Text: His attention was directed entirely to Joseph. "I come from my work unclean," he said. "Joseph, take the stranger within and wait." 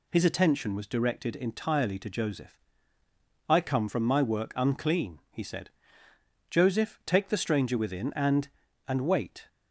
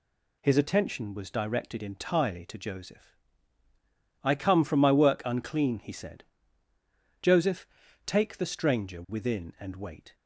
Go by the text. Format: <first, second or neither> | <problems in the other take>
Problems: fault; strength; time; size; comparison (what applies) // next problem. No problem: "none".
second | says "and" twice; at 8.8 s